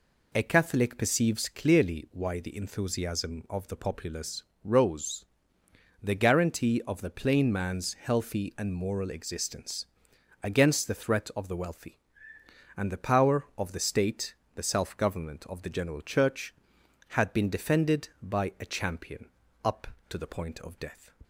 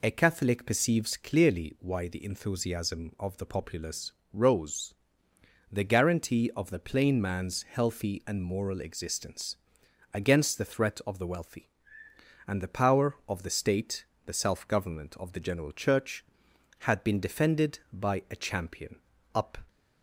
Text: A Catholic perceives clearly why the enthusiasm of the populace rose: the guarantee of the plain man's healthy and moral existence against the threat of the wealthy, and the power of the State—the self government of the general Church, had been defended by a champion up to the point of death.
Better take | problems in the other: first | pauses between "populace" and "rose"; slight; at 4.1 s; 0.18 s long; slight in the first // pauses between "existence" and "against"; noticeable; at 9.5 s; 0.56 s long; noticeable in the first // pauses between "champion" and "up"; slight; at 18.9 s; 0.36 s long; slight in the first // stops before "to the point of death"; at 19.6 s

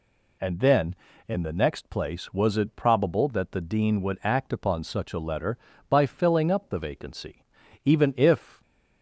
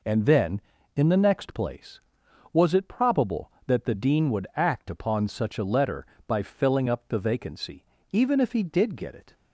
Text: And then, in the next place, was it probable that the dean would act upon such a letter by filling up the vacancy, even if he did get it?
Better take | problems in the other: second | stops before "he did get it"; at 8.6 s

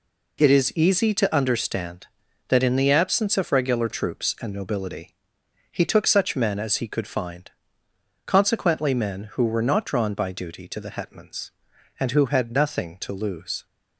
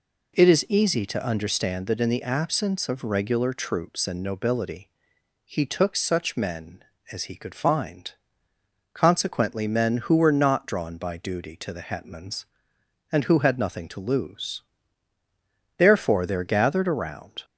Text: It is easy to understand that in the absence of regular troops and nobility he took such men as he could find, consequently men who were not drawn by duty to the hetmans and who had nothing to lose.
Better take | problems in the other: first | pauses between "nobility" and "he"; noticeable; at 4.8 s; 0.56 s long; noticeable in the first // goes on to say "Therefore there gathered around"; strong; from 15.7 s on; 1.6 s long

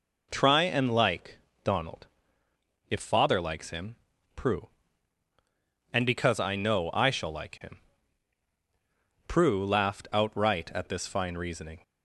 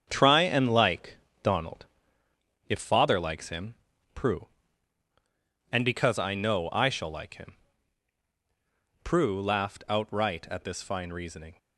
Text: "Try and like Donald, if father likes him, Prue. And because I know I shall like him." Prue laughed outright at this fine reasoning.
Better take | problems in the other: first | gets quieter; strong; throughout; 7.5 dB // pauses between "like" and "Donald"; slight; at 1.1 s; 0.24 s long; slight in the first

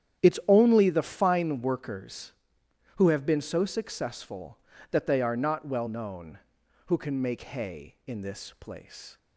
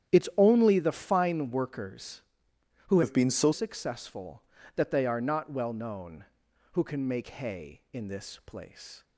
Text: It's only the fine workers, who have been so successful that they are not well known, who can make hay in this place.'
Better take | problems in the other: first | starts louder than the rest; strong; until 1.2 s; 10 dB; strong in the first // changes voice from "have" to "so"; from 3.0 to 3.5 s; 0.5 s long

